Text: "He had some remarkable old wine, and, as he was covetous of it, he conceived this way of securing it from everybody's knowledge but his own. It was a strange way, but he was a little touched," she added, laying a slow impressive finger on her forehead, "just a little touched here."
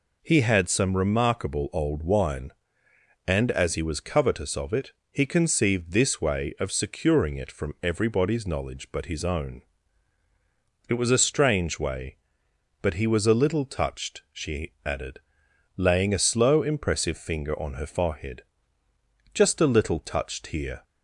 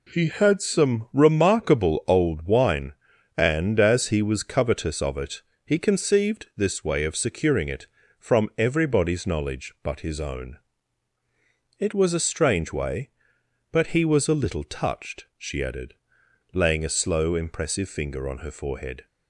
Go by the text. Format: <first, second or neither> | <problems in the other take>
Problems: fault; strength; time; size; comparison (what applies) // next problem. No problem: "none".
first | stops before "just a little touched here"; at 19.0 s